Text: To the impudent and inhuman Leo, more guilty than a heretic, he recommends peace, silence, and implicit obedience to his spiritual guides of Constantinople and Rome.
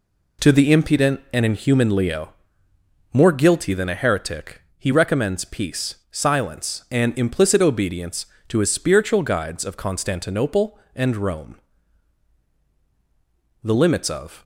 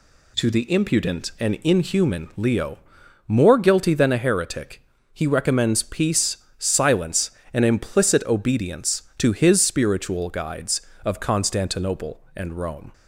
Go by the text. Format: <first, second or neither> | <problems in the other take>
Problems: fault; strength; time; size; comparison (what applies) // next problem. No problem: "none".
second | goes on to say "The limits of"; noticeable; from 13.6 s on; 0.78 s long